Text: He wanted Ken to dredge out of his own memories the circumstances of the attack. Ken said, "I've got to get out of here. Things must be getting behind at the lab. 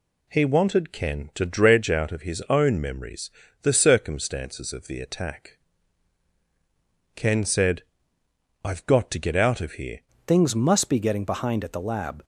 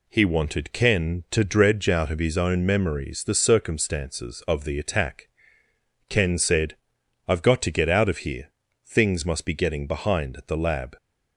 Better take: second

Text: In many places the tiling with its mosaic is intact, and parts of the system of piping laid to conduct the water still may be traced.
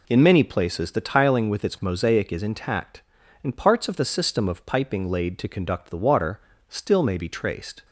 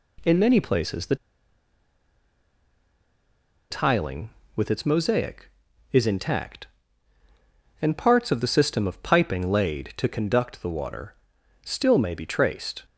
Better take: first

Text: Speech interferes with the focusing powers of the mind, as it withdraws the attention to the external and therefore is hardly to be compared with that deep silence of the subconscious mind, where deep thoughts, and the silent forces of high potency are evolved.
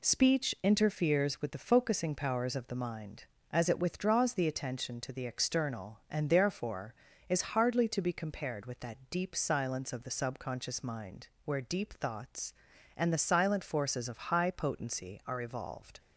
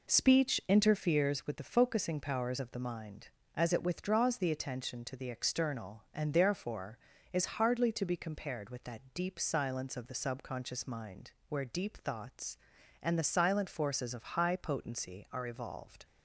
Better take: first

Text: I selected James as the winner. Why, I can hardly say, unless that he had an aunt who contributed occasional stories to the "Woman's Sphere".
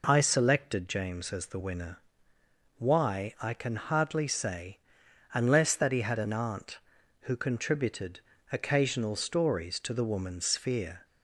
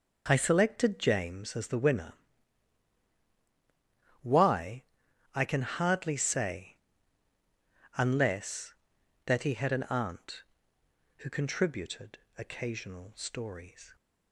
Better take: first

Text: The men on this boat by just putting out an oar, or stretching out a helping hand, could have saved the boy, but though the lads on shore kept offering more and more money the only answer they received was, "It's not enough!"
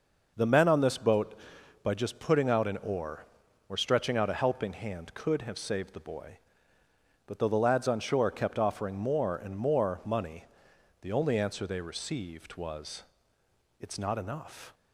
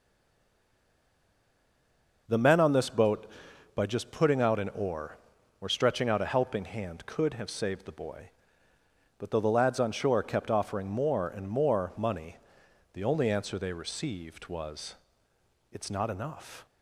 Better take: first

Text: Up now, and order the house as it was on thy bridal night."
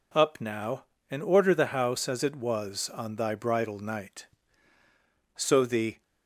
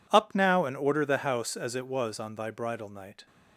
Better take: second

